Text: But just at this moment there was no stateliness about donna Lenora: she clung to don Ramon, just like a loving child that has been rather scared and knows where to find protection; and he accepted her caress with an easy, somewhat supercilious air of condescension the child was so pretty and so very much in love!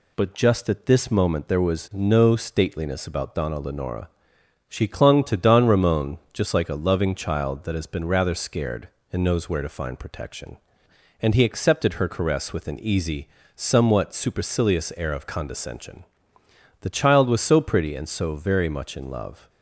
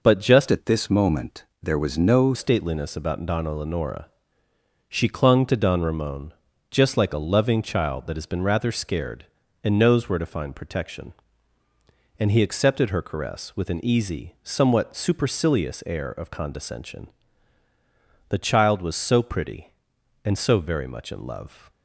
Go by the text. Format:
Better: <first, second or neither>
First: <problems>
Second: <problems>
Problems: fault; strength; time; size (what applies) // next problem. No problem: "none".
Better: first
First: pauses between "condescension" and "the"; noticeable; at 16.0 s; 0.78 s long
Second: changes voice from "at" to "no"; from 0.5 to 2.3 s; 1.8 s long // pauses between "moment" and "there"; slight; at 1.4 s; 0.18 s long // pauses between "condescension" and "the"; at 17.0 s; 1.2 s long